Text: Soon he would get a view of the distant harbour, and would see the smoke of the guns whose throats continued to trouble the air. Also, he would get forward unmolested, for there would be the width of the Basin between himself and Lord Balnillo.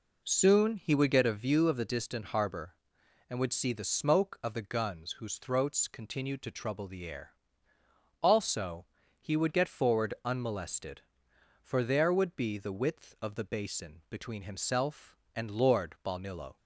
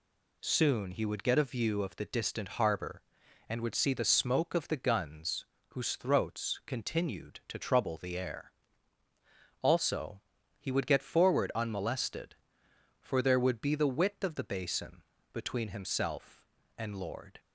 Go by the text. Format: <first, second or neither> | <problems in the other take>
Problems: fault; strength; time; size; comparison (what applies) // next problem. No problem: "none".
first | pauses between "guns" and "whose"; slight; at 5.4 s; 0.28 s long // pauses between "Basin" and "between"; slight; at 15.0 s; 0.30 s long // stops before "Balnillo"; at 17.3 s